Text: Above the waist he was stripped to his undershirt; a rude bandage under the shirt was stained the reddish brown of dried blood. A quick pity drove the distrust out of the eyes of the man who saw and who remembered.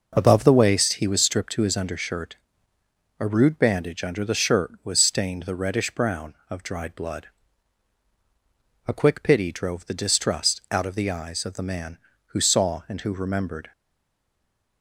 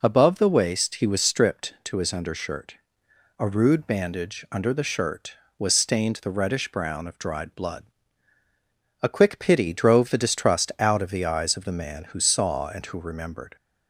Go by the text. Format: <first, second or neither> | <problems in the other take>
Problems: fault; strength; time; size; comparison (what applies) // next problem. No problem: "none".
second | stays silent after the last word; from 13.7 s on; 1.1 s long